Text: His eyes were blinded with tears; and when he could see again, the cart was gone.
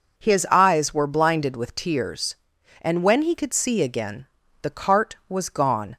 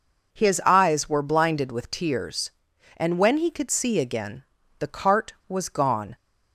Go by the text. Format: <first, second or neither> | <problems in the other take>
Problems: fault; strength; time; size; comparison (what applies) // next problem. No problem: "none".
neither | none